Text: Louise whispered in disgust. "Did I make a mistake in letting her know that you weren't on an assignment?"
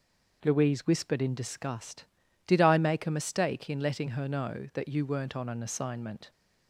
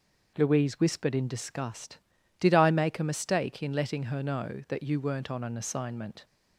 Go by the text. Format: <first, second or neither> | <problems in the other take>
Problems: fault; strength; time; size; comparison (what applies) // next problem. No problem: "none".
neither | none